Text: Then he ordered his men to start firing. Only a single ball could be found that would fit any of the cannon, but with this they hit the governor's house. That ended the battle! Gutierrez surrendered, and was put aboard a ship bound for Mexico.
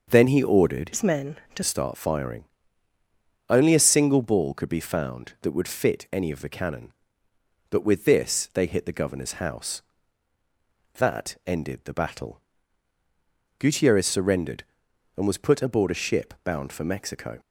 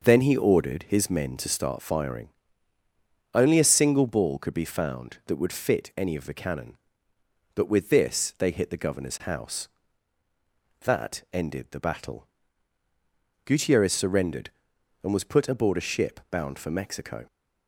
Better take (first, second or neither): second